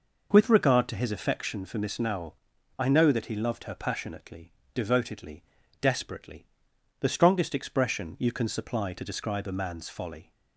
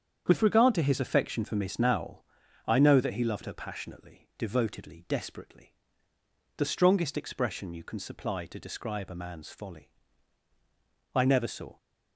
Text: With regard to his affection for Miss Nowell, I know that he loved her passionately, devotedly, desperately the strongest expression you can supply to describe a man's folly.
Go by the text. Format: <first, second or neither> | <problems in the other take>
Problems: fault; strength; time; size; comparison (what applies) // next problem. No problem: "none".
first | starts louder than the rest; strong; until 1.2 s; 8 dB // pauses between "desperately" and "the"; noticeable; at 5.7 s; 0.84 s long; noticeable in the first // goes on to say "I never saw"; noticeable; from 11.1 s on; 0.62 s long